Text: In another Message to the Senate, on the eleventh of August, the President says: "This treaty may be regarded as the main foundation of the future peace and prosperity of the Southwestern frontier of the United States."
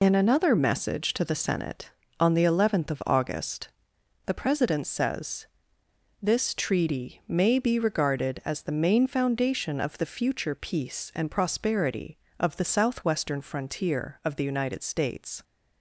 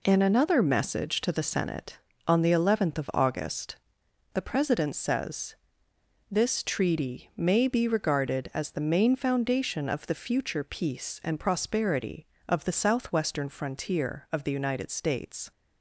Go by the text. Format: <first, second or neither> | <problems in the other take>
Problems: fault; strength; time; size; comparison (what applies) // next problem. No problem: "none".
second | loses the start of "In"; at 0.0 s; 45 ms